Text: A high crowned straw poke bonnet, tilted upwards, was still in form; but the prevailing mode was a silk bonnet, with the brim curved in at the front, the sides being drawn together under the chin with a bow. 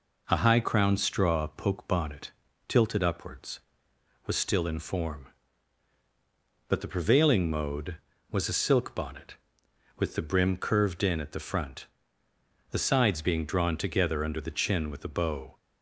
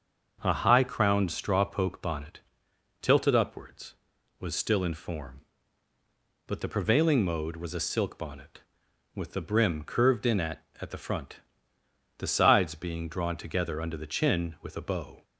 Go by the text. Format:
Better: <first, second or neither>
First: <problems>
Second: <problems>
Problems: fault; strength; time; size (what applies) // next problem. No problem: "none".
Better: first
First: none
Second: starts louder than the rest; until 1.4 s; 6.5 dB // says "at" twice; at 10.7 s